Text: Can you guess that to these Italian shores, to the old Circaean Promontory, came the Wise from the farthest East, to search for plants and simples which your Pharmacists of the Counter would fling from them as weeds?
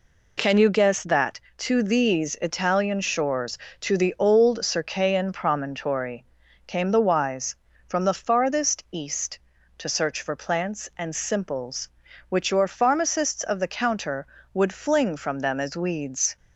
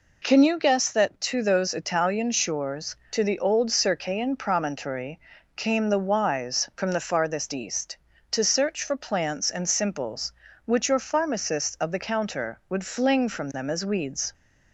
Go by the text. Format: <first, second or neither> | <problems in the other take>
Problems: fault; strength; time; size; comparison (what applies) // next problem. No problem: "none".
first | says "those" for "these"; at 1.4 s